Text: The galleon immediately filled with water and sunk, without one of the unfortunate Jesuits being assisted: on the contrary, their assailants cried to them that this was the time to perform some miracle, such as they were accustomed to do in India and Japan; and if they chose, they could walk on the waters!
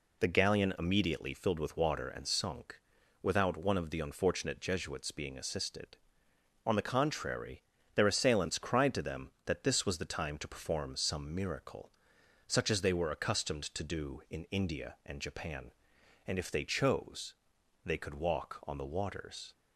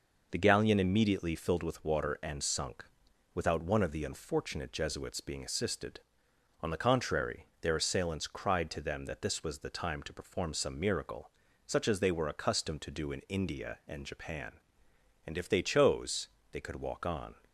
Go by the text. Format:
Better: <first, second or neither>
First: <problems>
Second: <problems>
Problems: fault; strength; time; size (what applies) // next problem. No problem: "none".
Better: first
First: none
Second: stops before "the waters"; at 17.4 s